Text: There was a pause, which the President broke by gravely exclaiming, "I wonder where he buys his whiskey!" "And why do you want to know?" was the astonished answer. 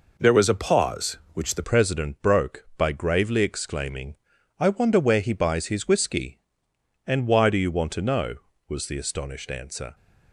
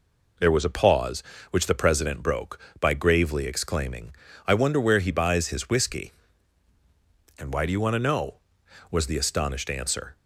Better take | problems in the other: second | changes voice at "President"; from 1.6 s on; 8.3 s long

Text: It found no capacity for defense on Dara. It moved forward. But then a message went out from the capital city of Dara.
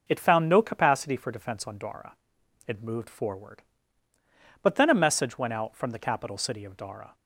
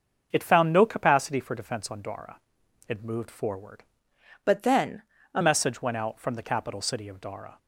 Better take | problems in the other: first | starts louder than the rest; until 1.3 s; 6.5 dB // changes voice from "But" to "a"; from 4.4 to 5.4 s; 1.0 s long // pauses between "then" and "a"; slight; at 5.0 s; 0.30 s long

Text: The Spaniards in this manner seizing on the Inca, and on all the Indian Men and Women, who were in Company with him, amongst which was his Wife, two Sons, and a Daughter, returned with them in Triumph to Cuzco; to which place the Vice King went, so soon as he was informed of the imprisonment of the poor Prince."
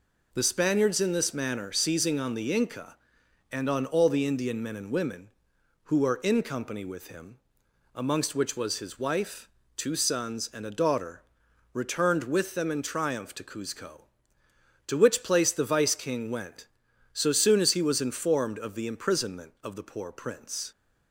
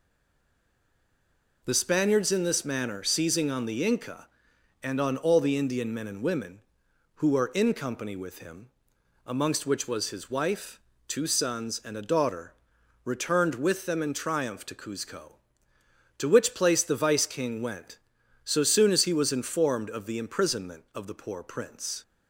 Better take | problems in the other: first | stays silent before the first word; noticeable; until 1.6 s; 1.6 s long

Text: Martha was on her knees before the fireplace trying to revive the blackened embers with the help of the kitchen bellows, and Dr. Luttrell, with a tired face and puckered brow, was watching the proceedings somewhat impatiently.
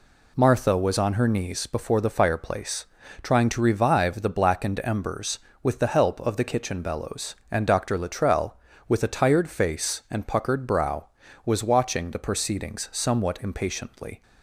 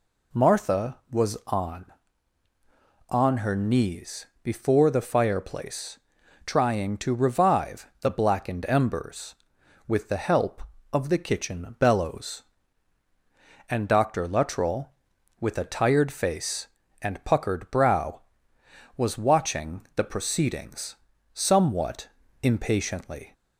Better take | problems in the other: first | says "on" twice; at 3.0 s // pauses between "knees" and "before"; slight; at 4.2 s; 0.18 s long // pauses between "fireplace" and "trying"; noticeable; at 5.9 s; 0.46 s long; slight in the first // pauses between "proceedings" and "somewhat"; at 20.9 s; 0.38 s long // pauses between "somewhat" and "impatiently"; slight; at 22.0 s; 0.34 s long

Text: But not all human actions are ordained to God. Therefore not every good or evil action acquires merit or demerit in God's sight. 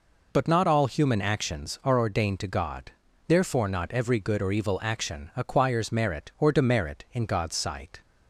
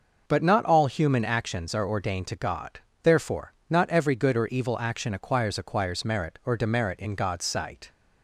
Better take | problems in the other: first | pauses between "Therefore" and "not"; slight; at 3.5 s; 0.16 s long // says "acquires" twice; at 5.5 s

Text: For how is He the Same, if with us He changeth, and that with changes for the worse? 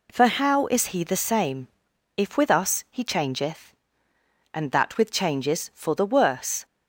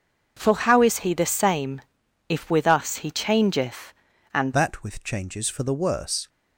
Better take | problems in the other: first | starts louder than the rest; until 1.3 s; 6.5 dB // changes voice at "that"; from 4.5 s on; 1.7 s long

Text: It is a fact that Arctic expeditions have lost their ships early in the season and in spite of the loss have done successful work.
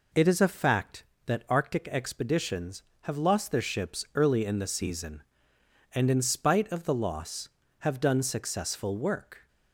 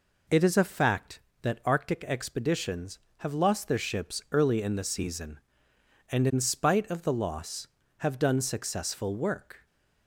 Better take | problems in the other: neither | none

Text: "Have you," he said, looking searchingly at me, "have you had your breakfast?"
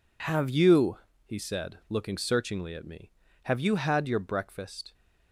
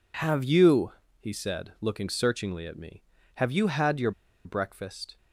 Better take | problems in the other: first | pauses between "your" and "breakfast"; slight; at 4.1 s; 0.33 s long

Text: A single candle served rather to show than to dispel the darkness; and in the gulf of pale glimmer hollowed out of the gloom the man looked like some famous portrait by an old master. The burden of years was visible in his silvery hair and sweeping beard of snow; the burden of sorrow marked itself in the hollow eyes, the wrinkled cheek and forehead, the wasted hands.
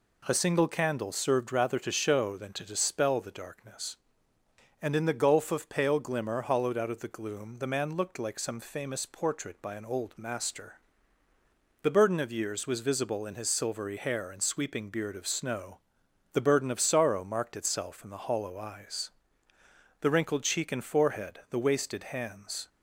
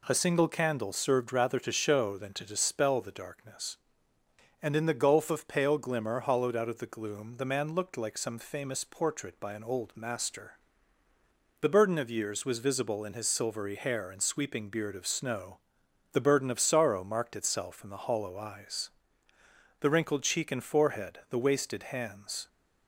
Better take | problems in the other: neither | none

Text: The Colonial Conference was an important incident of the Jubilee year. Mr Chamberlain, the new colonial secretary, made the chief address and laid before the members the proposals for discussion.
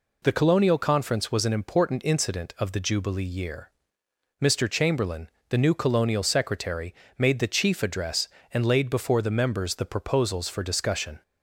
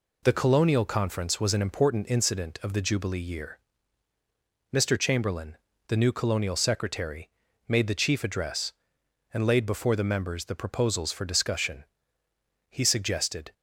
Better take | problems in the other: first | goes on to say "He suggested"; noticeable; from 12.6 s on; 0.84 s long

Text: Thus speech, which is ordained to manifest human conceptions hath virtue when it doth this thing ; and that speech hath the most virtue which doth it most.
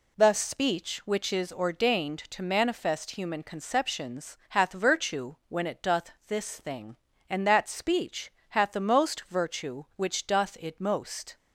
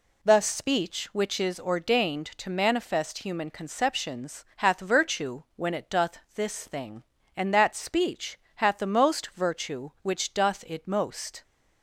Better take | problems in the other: neither | pauses between "doth" and "this"; slight; the same in both // pauses between "speech" and "hath"; slight; the same in both

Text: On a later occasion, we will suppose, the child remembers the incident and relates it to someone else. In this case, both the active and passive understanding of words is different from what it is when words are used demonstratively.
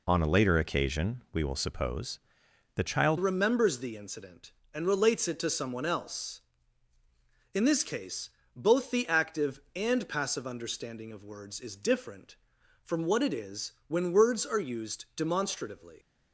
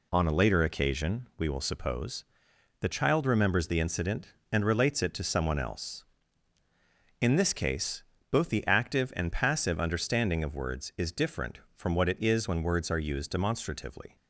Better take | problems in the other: second | changes voice at "remembers"; from 3.1 s on; 12.8 s long

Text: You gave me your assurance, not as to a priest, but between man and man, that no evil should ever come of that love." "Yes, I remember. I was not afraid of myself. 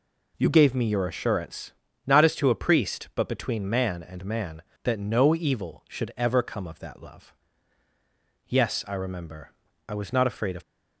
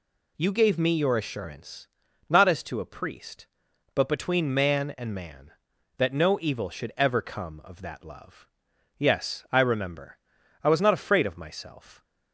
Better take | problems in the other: second | stops before "myself"; at 10.6 s

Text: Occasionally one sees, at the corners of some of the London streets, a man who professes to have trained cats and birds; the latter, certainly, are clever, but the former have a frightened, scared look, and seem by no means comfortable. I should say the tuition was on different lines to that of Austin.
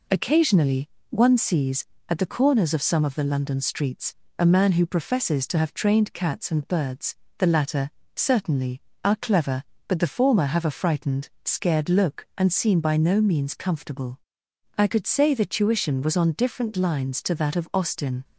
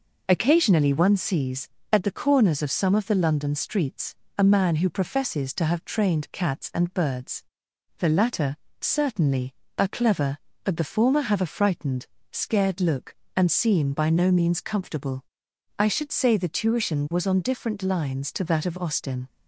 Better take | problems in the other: second | pauses between "Occasionally" and "one"; slight; at 0.8 s; 0.22 s long // says "could" for "should"; at 14.8 s

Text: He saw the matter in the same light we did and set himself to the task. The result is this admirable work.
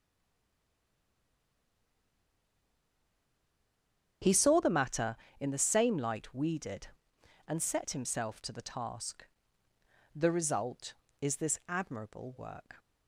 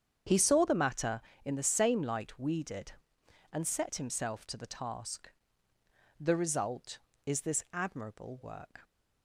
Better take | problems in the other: second | stays silent before the first word; strong; until 4.2 s; 4.2 s long // starts louder than the rest; strong; until 5.4 s; 8 dB; strong in the second

